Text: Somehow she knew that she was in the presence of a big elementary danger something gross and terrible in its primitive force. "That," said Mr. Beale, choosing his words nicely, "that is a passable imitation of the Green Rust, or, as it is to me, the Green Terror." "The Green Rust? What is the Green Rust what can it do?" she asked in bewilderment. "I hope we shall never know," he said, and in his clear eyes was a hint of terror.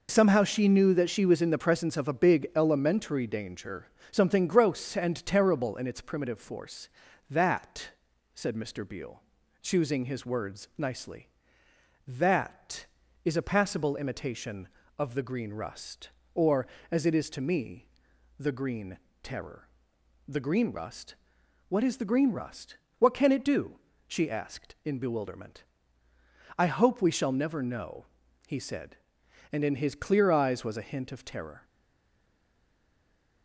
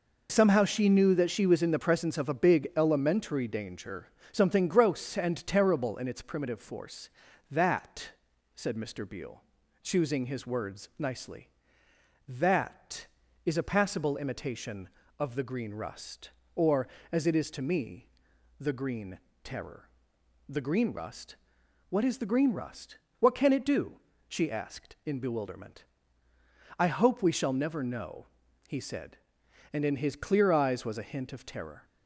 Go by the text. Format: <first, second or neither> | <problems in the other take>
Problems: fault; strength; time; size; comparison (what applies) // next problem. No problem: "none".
second | pauses between "danger" and "something"; slight; at 3.8 s; 0.24 s long; slight in the second // pauses between "Green" and "Terror"; slight; at 18.9 s; 0.24 s long; slight in the second // pauses between "Rust" and "what"; slight; at 22.7 s; 0.20 s long; slight in the second // stays silent after the last word; noticeable; from 31.6 s on; 1.8 s long